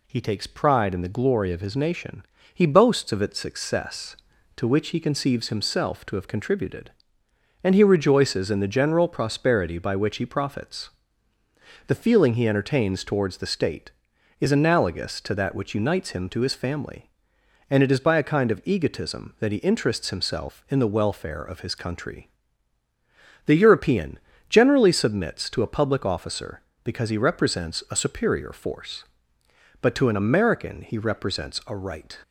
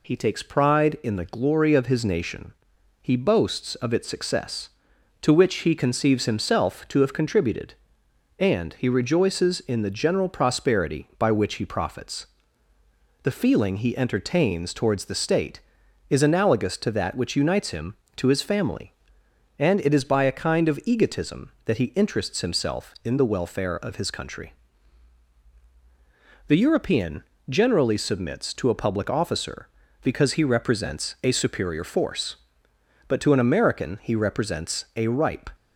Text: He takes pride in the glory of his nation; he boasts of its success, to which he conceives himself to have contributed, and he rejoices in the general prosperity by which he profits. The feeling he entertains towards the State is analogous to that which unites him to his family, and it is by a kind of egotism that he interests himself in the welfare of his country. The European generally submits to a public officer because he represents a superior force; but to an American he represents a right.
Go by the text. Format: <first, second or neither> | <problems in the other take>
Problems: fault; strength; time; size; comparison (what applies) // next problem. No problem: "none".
first | pauses between "European" and "generally"; slight; at 27.2 s; 0.26 s long; slight in the first // says "ripe" for "right"; at 35.0 s